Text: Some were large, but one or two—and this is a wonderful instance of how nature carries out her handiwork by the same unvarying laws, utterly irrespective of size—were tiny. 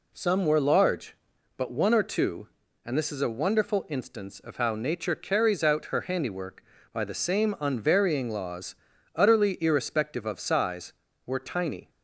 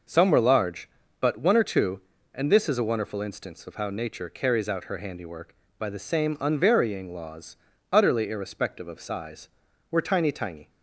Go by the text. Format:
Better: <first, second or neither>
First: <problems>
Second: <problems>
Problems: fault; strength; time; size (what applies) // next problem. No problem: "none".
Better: first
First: none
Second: says "tiny" twice; at 10.3 s